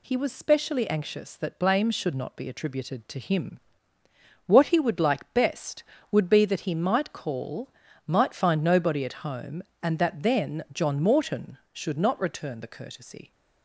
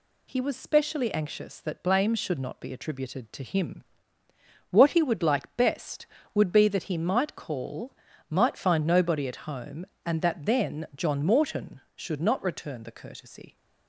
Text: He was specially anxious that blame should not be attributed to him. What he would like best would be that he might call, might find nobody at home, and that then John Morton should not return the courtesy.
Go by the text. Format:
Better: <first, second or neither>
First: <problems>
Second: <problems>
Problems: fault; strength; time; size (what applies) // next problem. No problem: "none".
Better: neither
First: none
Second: none